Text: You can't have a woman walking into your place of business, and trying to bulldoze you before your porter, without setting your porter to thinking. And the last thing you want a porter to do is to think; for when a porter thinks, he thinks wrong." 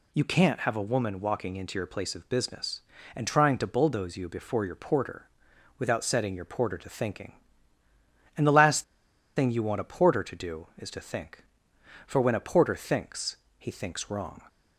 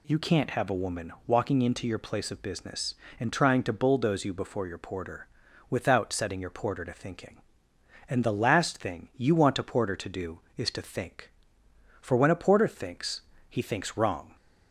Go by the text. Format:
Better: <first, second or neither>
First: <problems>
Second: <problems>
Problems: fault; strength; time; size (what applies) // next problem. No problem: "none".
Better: second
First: pauses between "last" and "thing"; noticeable; at 8.8 s; 0.53 s long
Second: none